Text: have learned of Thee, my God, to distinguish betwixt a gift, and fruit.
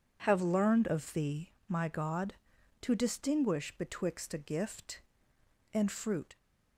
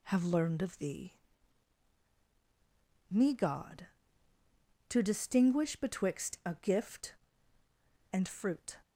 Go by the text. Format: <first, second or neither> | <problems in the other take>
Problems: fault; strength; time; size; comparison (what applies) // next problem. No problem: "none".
first | says "me" for "my"; at 3.1 s